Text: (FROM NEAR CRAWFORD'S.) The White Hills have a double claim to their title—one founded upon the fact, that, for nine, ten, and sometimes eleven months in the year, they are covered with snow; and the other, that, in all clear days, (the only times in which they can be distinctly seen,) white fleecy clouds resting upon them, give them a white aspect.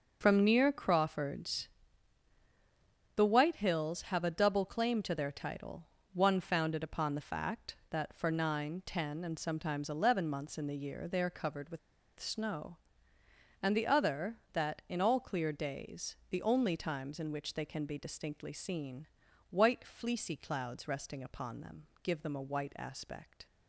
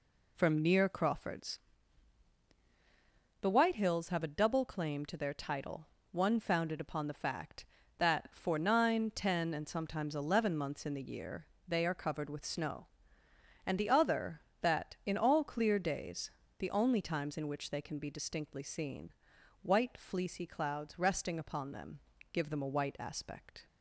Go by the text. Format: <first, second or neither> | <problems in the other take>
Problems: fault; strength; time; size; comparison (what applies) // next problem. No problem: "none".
second | pauses between "with" and "snow"; at 11.7 s; 0.40 s long